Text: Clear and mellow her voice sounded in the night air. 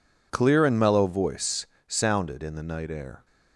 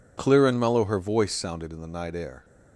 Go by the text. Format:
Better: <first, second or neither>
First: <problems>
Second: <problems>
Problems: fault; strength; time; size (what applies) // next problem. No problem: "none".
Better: second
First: skips "her"; at 1.0 s // pauses between "voice" and "sounded"; slight; at 1.6 s; 0.24 s long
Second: none